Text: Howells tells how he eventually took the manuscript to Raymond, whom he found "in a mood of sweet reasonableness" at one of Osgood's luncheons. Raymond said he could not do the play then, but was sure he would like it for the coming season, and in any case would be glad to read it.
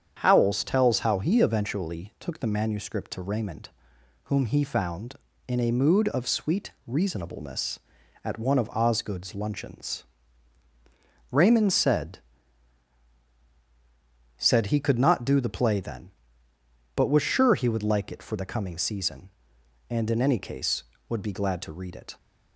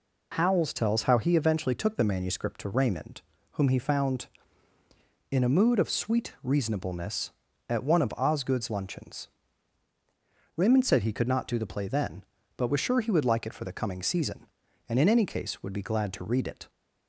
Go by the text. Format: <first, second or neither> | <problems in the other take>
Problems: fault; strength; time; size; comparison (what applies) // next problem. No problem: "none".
second | starts louder than the rest; strong; until 1.2 s; 8 dB // pauses between "sweet" and "reasonableness"; slight; at 6.7 s; 0.16 s long // says "said" twice; at 14.3 s